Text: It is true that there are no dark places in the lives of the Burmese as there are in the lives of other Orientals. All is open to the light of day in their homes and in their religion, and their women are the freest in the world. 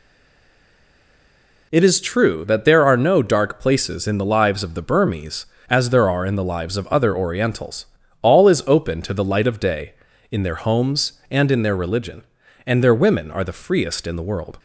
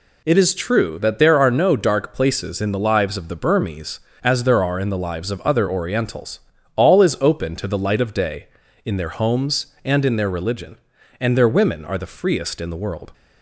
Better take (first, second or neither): second